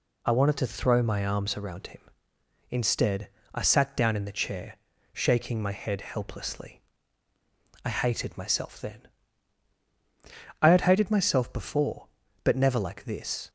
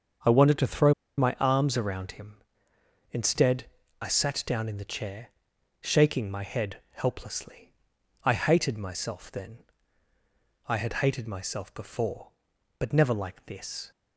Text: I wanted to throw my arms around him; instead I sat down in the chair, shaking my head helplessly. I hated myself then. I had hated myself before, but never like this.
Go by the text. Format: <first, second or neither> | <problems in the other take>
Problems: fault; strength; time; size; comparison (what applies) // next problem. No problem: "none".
first | starts louder than the rest; strong; until 1.5 s; 7 dB // pauses between "throw" and "my"; slight; at 0.9 s; 0.25 s long // pauses between "instead" and "I"; slight; at 3.6 s; 0.36 s long; slight in the first